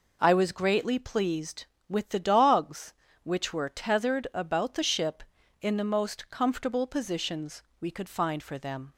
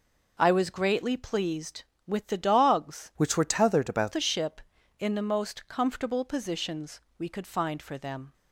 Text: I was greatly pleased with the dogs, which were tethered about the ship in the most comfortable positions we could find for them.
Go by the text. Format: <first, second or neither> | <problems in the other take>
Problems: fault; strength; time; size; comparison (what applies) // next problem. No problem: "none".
first | changes voice from "which" to "about"; from 3.1 to 4.1 s; 1.0 s long // pauses between "positions" and "we"; slight; at 7.0 s; 0.16 s long; slight in the first